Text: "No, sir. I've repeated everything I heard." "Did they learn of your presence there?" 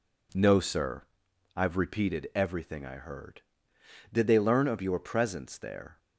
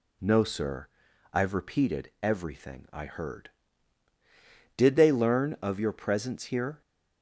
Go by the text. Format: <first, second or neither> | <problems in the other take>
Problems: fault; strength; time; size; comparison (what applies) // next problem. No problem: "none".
first | says "here" for "there"; at 6.4 s